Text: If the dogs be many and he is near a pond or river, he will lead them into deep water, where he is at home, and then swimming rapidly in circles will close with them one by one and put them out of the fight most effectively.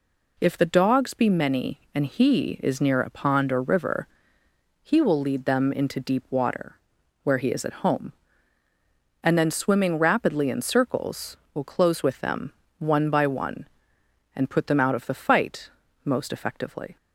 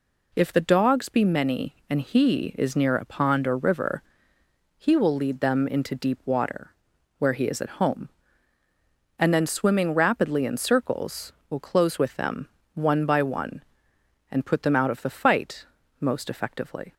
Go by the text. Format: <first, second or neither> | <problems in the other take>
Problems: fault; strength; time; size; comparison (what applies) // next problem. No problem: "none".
neither | pauses between "them" and "one"; slight; the same in both // pauses between "fight" and "most"; slight; the same in both